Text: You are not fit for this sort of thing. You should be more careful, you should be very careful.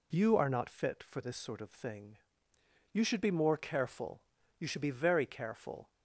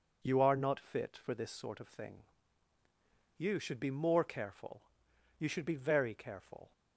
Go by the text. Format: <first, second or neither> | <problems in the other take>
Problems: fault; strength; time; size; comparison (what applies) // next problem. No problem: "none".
neither | none